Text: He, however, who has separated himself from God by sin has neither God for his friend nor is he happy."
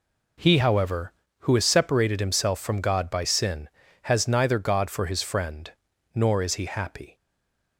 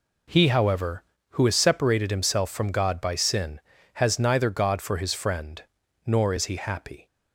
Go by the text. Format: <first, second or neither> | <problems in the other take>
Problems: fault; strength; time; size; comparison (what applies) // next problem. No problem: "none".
second | pauses between "friend" and "nor"; at 5.7 s; 0.42 s long; also in the second // stays silent after the last word; slight; from 7.1 s on; 0.6 s long